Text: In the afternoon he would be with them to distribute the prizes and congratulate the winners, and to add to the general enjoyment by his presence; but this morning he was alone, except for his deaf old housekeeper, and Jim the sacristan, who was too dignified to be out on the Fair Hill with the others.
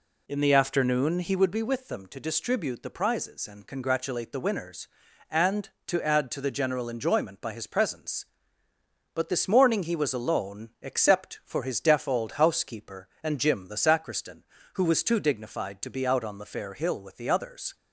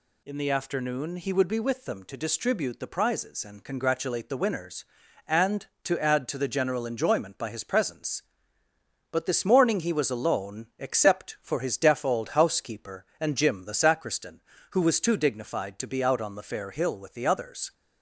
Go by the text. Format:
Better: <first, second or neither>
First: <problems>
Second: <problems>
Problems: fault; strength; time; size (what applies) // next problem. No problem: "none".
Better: second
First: starts louder than the rest; slight; until 1.4 s; 2 dB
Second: none